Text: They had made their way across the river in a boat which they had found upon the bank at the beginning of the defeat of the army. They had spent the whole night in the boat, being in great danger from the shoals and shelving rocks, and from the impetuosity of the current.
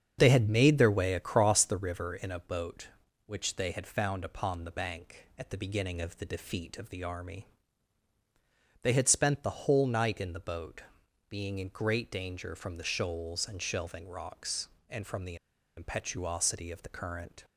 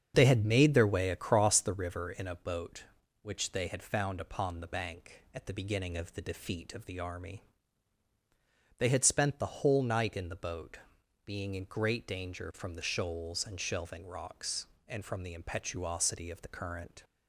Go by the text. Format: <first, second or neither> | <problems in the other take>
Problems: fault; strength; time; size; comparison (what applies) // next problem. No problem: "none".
second | starts louder than the rest; strong; until 1.2 s; 7.5 dB; strong in the second // pauses between "the" and "impetuosity"; at 15.3 s; 0.41 s long